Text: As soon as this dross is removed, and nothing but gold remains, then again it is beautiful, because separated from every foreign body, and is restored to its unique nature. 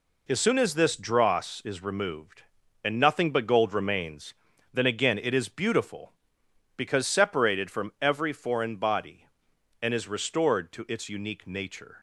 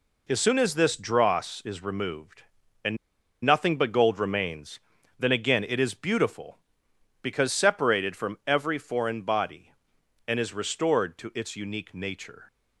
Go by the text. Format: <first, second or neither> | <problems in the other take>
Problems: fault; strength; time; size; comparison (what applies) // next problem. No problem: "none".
first | pauses between "and" and "nothing"; noticeable; at 2.9 s; 0.47 s long